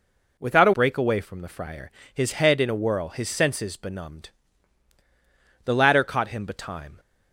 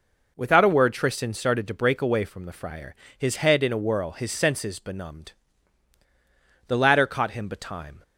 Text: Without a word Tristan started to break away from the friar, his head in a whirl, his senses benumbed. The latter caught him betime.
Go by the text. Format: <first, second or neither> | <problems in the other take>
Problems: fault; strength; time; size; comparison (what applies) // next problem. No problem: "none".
second | skips "word Tristan started to"; at 0.7 s